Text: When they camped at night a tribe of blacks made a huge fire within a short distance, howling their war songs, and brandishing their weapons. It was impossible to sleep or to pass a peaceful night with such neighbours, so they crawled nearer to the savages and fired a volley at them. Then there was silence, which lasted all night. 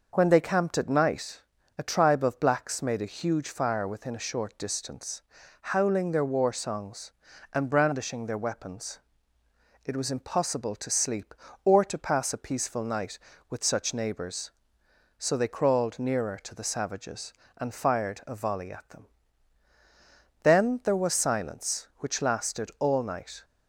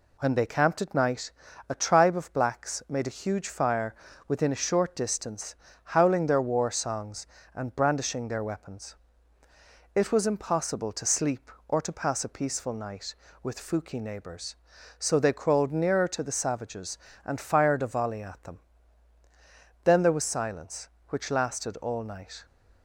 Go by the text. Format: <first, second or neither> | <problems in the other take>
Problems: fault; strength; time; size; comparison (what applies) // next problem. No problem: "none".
first | pauses between "night" and "a"; slight; at 1.3 s; 0.36 s long; slight in the first // pauses between "fire" and "within"; slight; at 3.9 s; 0.34 s long // says "fuki" for "such"; at 13.5 s